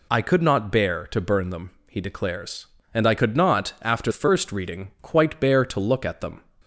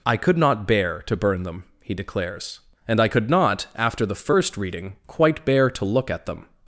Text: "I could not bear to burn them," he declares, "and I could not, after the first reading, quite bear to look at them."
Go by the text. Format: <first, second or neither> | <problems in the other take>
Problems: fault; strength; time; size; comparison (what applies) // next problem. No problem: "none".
second | skips "the"; at 4.1 s